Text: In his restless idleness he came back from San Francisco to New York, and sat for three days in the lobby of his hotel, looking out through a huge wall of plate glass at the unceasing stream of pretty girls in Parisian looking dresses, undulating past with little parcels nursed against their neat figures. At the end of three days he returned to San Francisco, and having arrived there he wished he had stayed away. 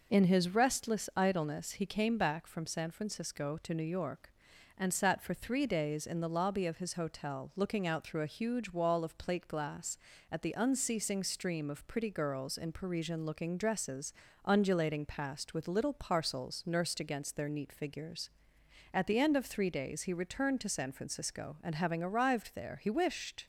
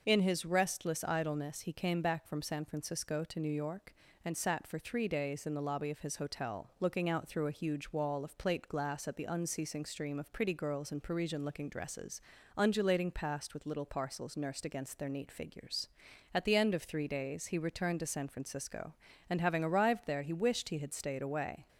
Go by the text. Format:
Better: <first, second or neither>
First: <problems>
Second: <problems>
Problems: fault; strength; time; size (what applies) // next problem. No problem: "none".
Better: second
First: stops before "he had stayed away"; at 23.4 s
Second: none